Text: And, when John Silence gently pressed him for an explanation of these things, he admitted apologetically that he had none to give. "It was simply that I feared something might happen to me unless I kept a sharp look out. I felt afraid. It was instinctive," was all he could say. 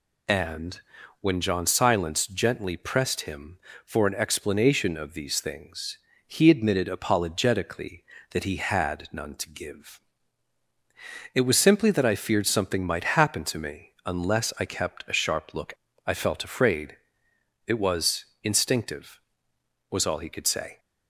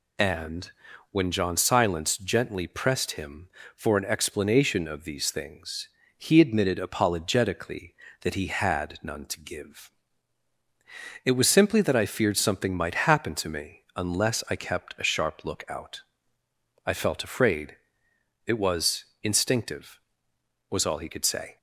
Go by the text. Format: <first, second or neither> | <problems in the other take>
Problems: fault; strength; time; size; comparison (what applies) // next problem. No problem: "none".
second | skips "out"; at 15.9 s // pauses between "was" and "instinctive"; slight; at 18.2 s; 0.18 s long; slight in the second